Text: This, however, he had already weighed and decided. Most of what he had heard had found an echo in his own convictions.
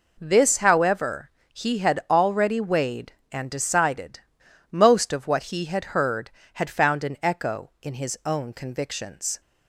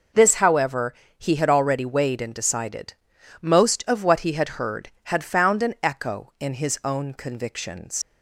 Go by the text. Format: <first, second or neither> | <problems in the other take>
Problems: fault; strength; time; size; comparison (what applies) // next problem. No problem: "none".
first | leaves "convictions" unfinished; at 8.0 s; 85 ms